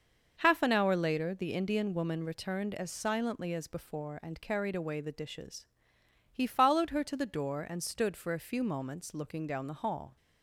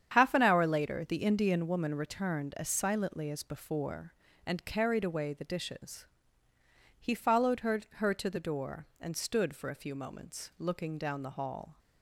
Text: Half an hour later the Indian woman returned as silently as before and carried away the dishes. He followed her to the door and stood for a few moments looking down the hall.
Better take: first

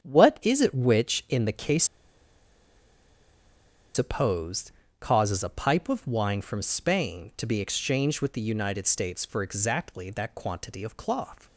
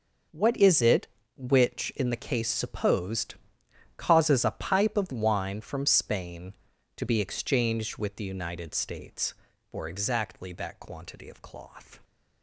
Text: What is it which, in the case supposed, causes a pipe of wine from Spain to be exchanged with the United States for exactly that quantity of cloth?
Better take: second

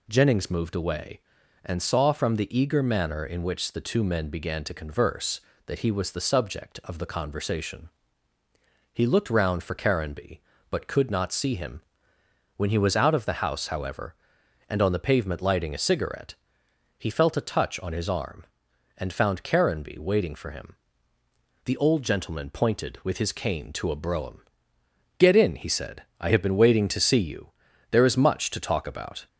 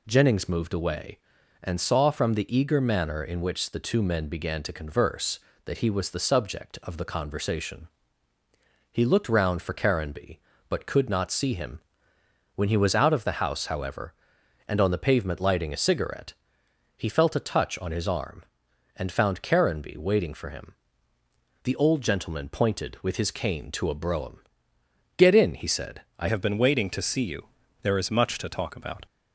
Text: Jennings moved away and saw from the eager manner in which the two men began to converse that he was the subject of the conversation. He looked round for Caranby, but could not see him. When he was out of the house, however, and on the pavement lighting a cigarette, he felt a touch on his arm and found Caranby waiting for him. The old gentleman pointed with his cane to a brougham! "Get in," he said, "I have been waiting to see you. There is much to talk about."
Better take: first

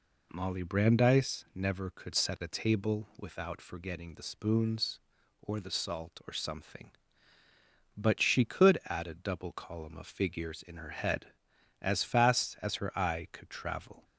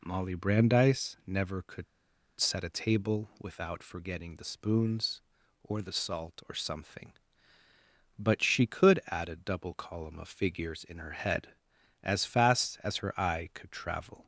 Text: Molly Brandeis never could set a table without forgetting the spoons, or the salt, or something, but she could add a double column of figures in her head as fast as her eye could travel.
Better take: first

